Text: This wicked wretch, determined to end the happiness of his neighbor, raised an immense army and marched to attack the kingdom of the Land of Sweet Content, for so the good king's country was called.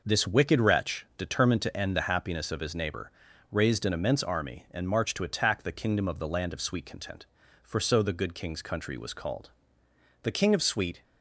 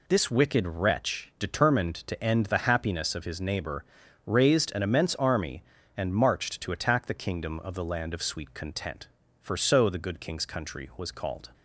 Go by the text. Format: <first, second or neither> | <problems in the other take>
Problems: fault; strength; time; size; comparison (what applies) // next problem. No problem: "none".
second | goes on to say "The king of Sweet"; noticeable; from 10.2 s on; 0.80 s long